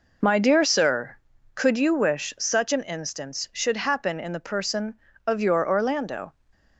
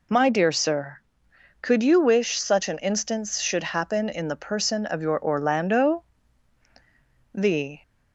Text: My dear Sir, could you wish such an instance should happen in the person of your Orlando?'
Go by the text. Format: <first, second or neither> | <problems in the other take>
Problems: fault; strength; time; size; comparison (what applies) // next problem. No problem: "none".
first | goes on to say "The"; slight; from 7.3 s on; 0.48 s long